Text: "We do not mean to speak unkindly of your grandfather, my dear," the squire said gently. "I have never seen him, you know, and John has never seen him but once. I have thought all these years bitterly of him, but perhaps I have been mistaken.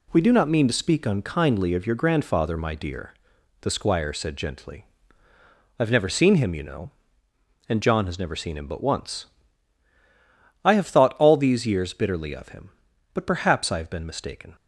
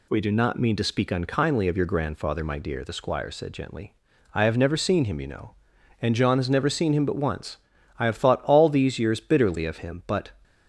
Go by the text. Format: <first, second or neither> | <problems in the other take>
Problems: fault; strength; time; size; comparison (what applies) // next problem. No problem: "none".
first | stops before "perhaps I have been mistaken"; at 10.4 s